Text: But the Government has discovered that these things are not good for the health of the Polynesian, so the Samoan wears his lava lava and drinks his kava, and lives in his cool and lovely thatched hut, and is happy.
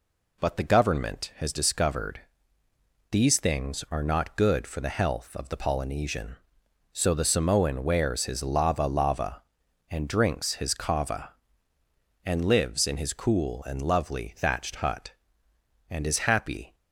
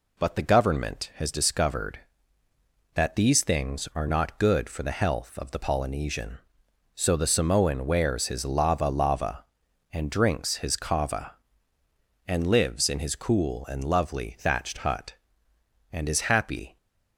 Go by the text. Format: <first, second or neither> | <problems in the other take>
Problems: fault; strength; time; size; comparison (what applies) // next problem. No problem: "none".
second | skips "that"; at 2.6 s